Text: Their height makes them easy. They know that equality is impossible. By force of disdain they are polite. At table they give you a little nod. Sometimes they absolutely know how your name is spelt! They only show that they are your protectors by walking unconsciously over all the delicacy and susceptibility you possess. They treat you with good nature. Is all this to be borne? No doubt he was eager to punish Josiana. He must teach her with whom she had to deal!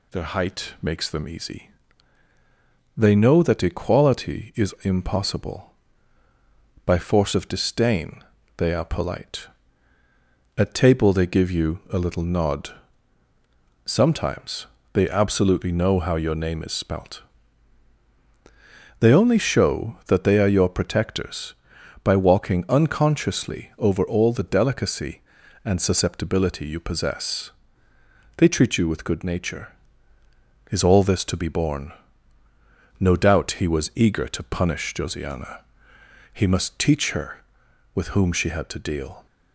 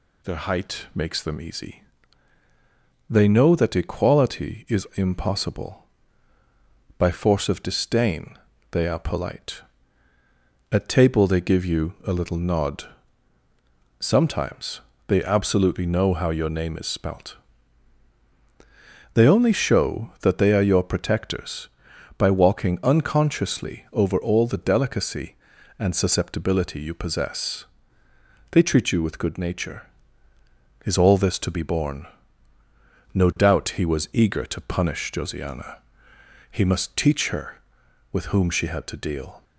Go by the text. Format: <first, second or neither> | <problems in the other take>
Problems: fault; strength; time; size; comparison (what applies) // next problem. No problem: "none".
neither | pauses between "disdain" and "they"; slight; the same in both // pauses between "Sometimes" and "they"; slight; the same in both